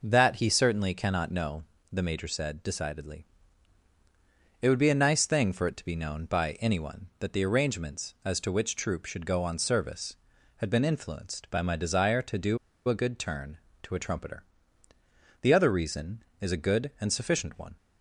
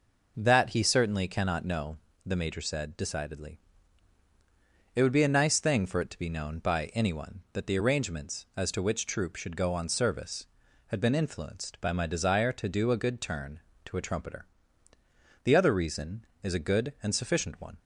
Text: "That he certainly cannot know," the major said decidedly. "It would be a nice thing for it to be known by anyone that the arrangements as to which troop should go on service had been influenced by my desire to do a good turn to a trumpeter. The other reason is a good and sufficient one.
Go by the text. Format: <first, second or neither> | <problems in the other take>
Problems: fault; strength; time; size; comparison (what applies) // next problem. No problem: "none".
second | pauses between "do" and "a"; slight; at 12.5 s; 0.31 s long